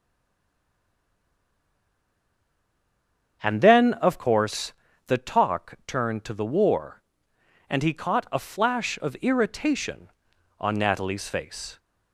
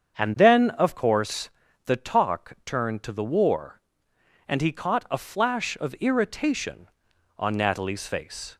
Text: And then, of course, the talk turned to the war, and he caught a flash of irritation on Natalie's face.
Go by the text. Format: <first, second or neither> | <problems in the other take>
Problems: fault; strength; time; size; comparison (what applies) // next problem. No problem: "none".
second | stays silent before the first word; strong; until 3.4 s; 3.4 s long // starts louder than the rest; strong; until 4.4 s; 7.5 dB; strong in the second